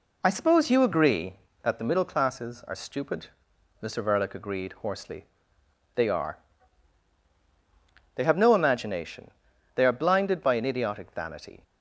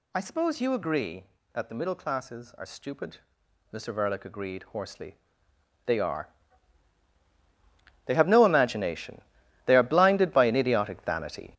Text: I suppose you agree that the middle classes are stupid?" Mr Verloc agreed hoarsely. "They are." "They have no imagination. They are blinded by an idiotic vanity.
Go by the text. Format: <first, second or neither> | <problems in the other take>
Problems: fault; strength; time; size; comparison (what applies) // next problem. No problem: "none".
first | gets louder; strong; throughout; 8.5 dB